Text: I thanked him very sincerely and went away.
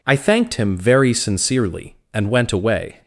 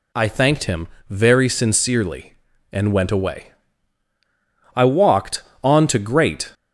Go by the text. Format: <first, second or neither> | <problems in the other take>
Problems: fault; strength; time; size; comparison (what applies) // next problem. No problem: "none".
first | pauses between "him" and "very"; slight; at 0.8 s; 0.20 s long // goes on to say "I walked on to Great"; strong; from 4.7 s on; 1.7 s long